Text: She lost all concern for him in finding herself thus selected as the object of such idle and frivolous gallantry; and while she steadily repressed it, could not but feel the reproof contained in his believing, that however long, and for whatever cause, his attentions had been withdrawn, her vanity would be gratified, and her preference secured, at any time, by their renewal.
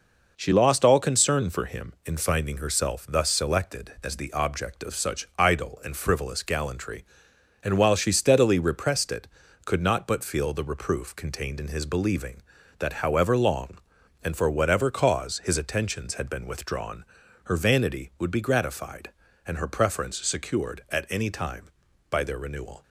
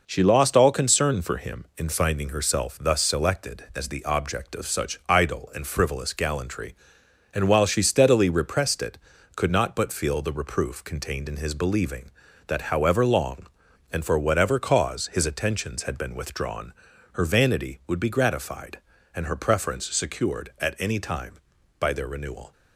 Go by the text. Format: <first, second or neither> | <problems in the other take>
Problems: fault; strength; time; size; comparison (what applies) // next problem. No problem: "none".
neither | none